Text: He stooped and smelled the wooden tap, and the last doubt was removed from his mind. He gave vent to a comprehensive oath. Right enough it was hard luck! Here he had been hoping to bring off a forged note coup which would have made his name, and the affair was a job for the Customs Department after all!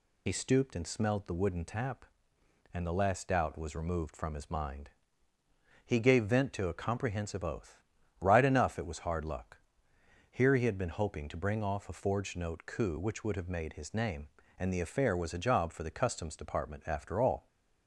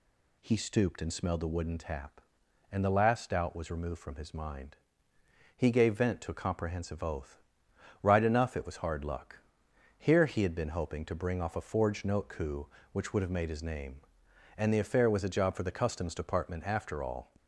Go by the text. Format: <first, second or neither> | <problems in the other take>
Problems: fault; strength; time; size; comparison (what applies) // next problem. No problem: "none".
second | loses the start of "He"; at 0.2 s; 50 ms